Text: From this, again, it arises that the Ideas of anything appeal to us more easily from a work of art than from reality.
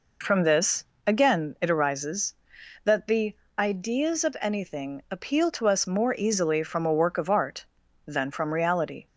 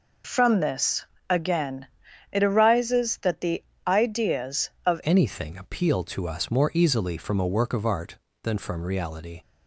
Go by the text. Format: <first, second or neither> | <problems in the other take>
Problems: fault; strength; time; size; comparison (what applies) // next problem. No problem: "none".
first | pauses between "the" and "Ideas"; slight; at 3.6 s; 0.24 s long; slight in the first // changes voice at "anything"; from 5.0 s on; 4.4 s long